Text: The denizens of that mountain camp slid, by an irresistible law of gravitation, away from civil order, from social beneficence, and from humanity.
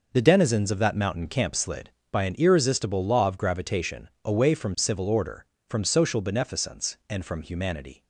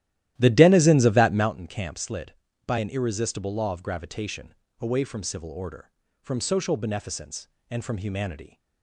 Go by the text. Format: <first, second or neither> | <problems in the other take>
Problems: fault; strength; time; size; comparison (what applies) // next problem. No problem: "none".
first | starts louder than the rest; strong; until 1.6 s; 13.5 dB